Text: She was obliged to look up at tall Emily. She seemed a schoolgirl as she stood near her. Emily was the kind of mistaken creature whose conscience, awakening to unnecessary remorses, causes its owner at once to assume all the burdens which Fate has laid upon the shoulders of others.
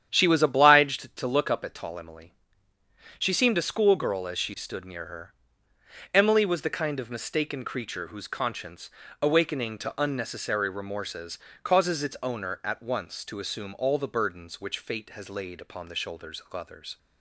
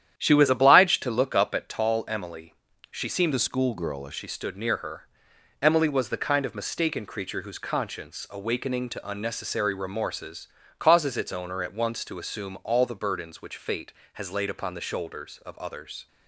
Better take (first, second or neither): first